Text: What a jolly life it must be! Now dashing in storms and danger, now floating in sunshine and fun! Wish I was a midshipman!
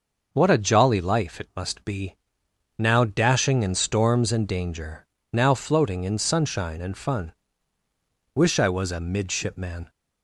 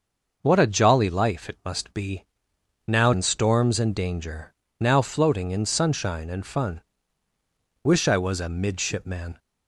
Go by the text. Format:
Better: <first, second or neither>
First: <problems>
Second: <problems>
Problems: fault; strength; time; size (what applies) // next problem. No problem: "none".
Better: first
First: none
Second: skips "dashing"; at 3.1 s